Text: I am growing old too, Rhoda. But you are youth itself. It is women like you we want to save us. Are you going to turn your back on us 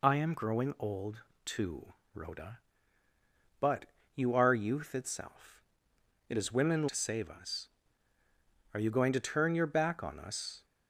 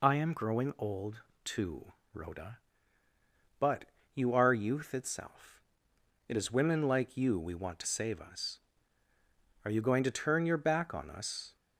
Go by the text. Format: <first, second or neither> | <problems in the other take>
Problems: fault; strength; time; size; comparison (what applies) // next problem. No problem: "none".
second | pauses between "old" and "too"; slight; at 1.2 s; 0.20 s long; slight in the second // pauses between "But" and "you"; slight; at 3.8 s; 0.28 s long; slight in the second // skips "like you we want"; at 6.8 s